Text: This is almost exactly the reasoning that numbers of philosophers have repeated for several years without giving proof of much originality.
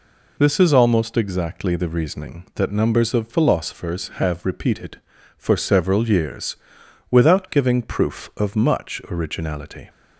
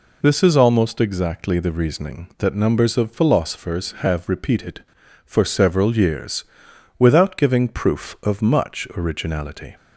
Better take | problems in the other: neither | pauses between "years" and "without"; noticeable; the same in both

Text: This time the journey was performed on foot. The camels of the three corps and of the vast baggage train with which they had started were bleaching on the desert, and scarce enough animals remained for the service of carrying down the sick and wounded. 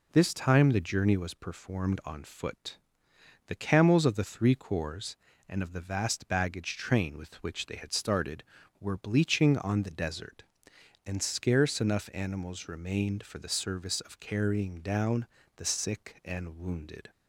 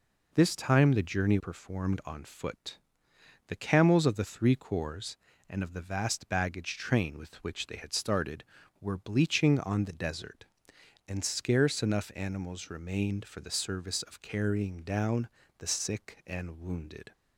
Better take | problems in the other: first | skips "was"; at 1.3 s // pauses between "down" and "the"; slight; at 15.2 s; 0.30 s long; slight in the first

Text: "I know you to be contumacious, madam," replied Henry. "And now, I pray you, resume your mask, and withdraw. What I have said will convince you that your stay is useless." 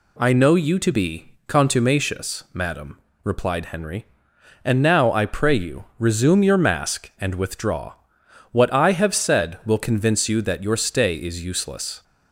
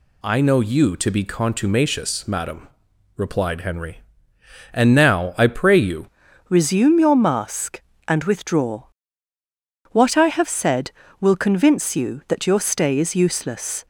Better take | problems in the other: first | changes voice at "resume"; from 6.4 s on; 7.4 s long

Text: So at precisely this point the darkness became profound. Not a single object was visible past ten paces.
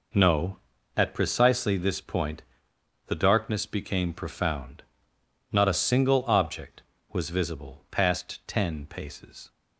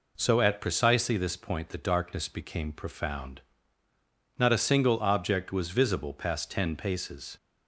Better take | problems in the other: second | says "No" for "So"; at 0.1 s // pauses between "point" and "the"; noticeable; at 2.4 s; 0.64 s long

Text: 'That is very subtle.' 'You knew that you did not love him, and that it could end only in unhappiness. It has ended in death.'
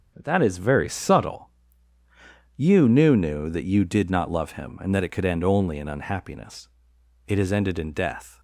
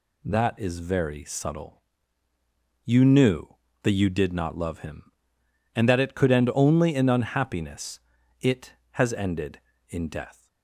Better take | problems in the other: second | starts louder than the rest; until 1.1 s; 6.5 dB // says "knew" twice; at 3.1 s

